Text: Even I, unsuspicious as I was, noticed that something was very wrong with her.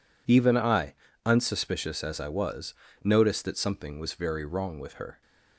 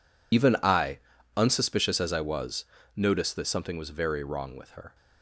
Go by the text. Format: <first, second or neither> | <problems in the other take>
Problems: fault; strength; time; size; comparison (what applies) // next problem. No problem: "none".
first | loses the start of "Even"; at 0.3 s; 55 ms